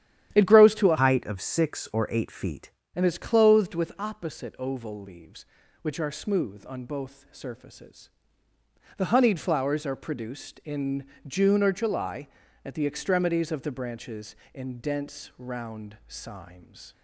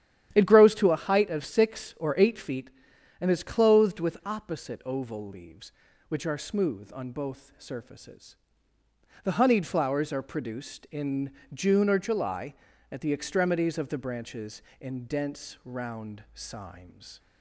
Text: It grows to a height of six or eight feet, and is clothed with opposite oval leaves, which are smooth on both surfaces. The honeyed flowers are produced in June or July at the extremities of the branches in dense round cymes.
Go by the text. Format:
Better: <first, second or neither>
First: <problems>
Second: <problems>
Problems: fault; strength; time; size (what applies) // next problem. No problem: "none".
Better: second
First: starts louder than the rest; strong; until 1.4 s; 11 dB // changes voice from "height" to "feet"; from 1.0 to 2.7 s; 1.7 s long // pauses between "in" and "June"; slight; at 11.0 s; 0.22 s long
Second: starts louder than the rest; strong; until 1.3 s; 11 dB // pauses between "in" and "June"; slight; at 11.3 s; 0.22 s long